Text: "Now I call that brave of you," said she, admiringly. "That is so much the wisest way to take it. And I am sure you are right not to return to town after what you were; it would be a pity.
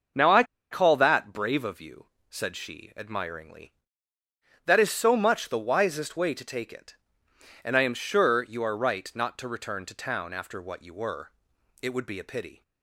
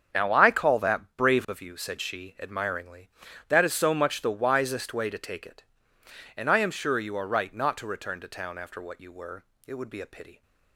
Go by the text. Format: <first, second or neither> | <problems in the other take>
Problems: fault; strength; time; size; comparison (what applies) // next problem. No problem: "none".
second | starts louder than the rest; until 1.4 s; 6 dB; strong in the second // pauses between "I" and "call"; slight; at 0.4 s; 0.27 s long